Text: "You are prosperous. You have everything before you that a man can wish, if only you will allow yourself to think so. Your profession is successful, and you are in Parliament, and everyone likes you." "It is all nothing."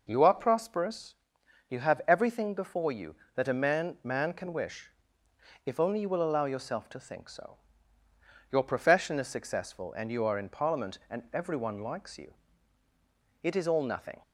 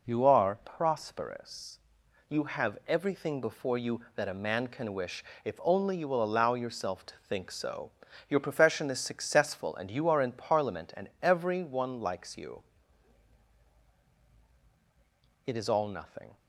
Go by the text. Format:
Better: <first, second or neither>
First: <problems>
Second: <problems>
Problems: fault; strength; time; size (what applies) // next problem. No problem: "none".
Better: second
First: says "man" twice; at 4.0 s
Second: none